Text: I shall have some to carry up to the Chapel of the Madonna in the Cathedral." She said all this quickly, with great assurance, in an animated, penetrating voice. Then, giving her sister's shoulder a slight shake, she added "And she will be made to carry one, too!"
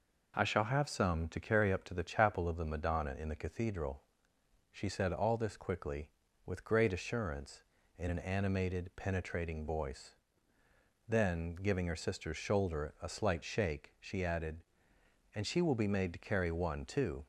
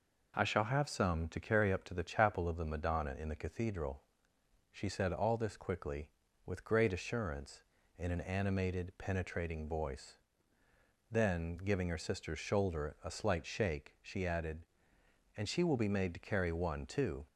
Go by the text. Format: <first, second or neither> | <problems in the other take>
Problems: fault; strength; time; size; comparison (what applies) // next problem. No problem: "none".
neither | none